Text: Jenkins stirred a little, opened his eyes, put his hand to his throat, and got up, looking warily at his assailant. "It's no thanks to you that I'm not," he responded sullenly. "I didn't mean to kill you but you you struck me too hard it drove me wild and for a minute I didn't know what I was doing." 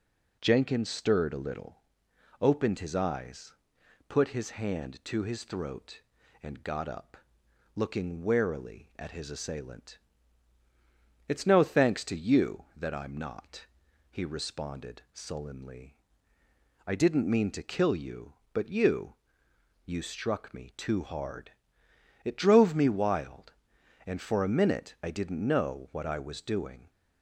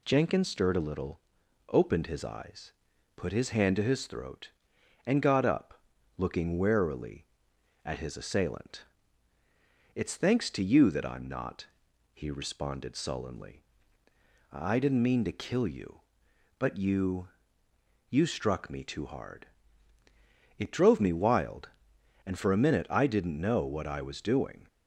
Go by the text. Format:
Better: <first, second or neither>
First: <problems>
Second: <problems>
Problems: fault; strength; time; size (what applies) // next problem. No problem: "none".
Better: first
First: pauses between "you" and "you"; noticeable; at 19.1 s; 0.70 s long // pauses between "hard" and "it"; noticeable; at 21.4 s; 0.74 s long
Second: skips "no"; at 10.1 s // pauses between "you" and "you"; noticeable; at 17.2 s; 0.80 s long // pauses between "hard" and "it"; at 19.4 s; 1.1 s long